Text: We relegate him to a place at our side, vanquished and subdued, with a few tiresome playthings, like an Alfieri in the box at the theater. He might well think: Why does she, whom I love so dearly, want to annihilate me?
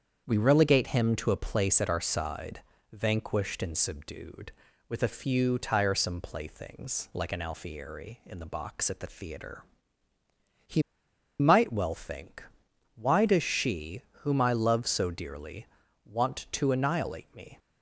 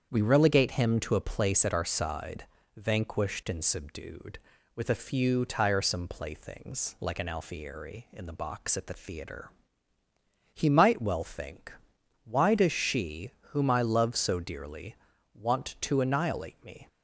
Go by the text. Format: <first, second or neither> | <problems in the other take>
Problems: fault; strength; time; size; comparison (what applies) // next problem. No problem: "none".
second | starts louder than the rest; strong; until 1.2 s; 7.5 dB; strong in the second // pauses between "He" and "might"; noticeable; at 10.8 s; 0.59 s long